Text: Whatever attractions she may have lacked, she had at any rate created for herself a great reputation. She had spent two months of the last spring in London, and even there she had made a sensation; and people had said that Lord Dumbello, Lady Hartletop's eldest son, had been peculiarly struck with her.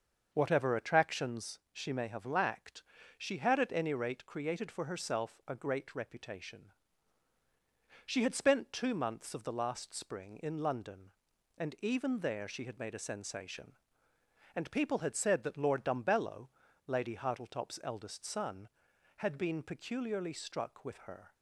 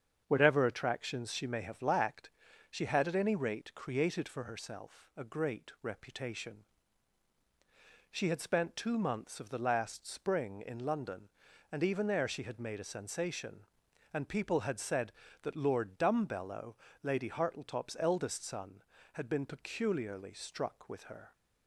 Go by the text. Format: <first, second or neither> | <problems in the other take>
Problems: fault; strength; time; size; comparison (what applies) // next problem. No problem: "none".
neither | starts louder than the rest; the same in both